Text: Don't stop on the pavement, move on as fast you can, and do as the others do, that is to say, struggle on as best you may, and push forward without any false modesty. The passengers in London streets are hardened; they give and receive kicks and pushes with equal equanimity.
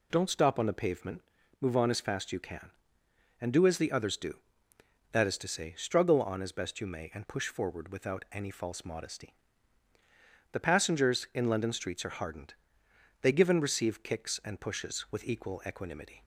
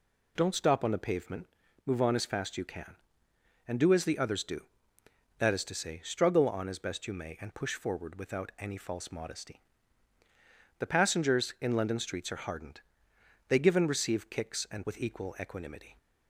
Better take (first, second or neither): first